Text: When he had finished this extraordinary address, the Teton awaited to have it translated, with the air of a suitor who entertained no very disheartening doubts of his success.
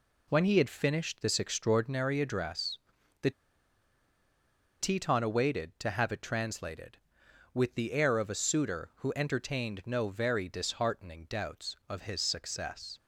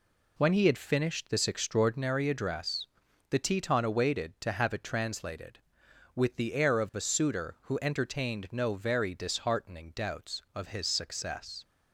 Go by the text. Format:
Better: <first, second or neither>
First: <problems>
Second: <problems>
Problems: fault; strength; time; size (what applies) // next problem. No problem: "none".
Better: second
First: pauses between "the" and "Teton"; strong; at 3.3 s; 1.4 s long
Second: none